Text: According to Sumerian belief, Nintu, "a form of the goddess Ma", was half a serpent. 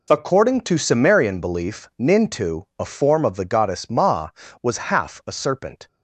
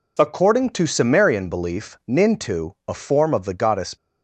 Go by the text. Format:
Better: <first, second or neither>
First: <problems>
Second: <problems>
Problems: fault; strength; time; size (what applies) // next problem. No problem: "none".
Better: first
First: none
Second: stops before "Ma was half a serpent"; at 3.9 s